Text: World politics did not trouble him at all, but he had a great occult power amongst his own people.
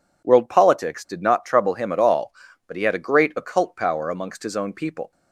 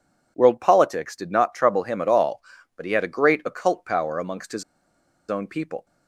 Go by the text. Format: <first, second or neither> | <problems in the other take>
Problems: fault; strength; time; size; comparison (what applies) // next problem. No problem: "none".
first | pauses between "his" and "own"; noticeable; at 4.6 s; 0.65 s long